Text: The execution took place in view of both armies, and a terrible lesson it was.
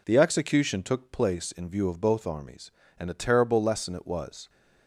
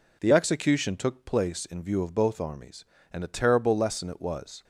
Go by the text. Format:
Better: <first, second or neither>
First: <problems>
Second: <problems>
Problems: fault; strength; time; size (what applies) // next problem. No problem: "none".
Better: neither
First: none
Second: none